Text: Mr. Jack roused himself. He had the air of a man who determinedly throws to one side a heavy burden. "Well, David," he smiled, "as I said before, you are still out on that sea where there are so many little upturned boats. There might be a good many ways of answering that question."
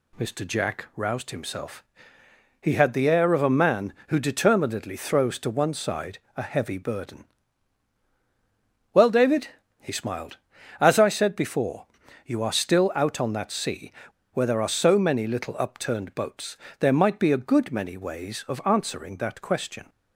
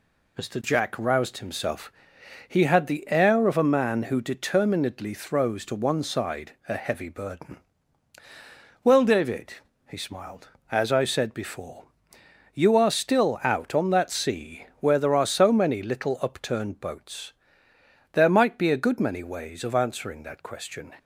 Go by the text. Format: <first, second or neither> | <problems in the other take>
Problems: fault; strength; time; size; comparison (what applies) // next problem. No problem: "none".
second | pauses between "side" and "a"; slight; at 6.1 s; 0.18 s long; slight in the second // pauses between "sea" and "where"; at 13.9 s; 0.40 s long